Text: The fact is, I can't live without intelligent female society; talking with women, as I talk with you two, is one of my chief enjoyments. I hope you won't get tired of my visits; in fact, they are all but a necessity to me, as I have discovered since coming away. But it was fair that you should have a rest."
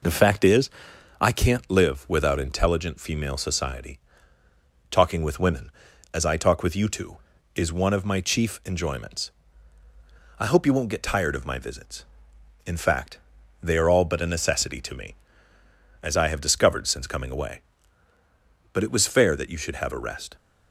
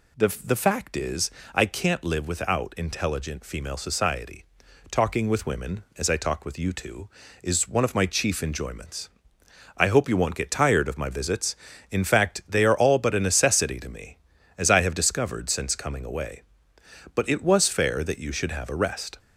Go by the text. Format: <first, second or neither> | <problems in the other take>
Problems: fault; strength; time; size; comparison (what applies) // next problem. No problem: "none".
first | says "The" twice; at 0.4 s